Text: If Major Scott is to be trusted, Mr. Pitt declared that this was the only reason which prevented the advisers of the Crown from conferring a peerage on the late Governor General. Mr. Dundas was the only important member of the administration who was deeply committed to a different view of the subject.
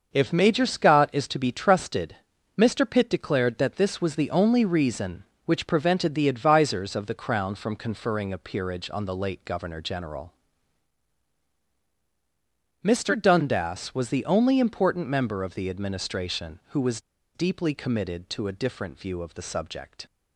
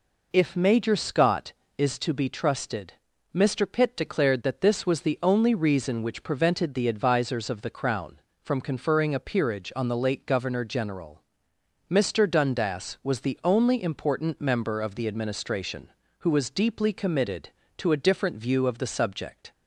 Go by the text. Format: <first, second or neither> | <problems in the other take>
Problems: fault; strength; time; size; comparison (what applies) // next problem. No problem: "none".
second | starts louder than the rest; until 1.1 s; 6 dB // pauses between "was" and "deeply"; slight; at 17.0 s; 0.34 s long